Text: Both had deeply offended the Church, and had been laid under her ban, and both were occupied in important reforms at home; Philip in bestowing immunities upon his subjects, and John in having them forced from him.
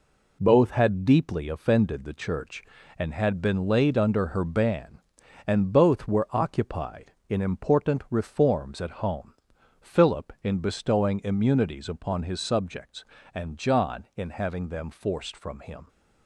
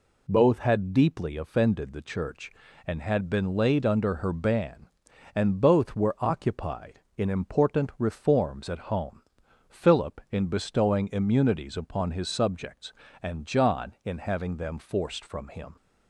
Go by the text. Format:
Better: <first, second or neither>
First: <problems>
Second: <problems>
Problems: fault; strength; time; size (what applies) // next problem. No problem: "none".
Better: second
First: gets quieter; throughout; 6 dB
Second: none